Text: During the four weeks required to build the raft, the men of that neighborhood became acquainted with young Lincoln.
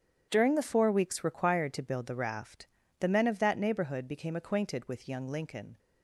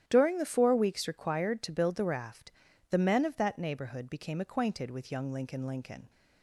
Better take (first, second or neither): first